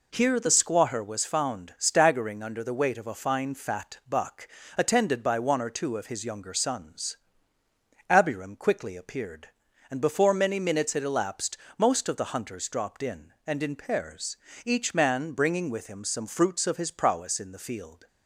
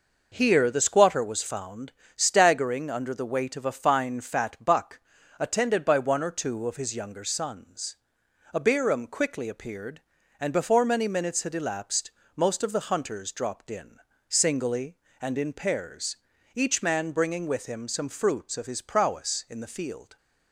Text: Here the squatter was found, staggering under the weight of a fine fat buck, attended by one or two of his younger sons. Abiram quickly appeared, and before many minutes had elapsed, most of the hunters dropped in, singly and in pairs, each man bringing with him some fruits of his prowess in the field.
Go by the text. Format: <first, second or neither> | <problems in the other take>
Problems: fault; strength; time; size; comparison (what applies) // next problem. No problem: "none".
second | skips "singly"; at 13.3 s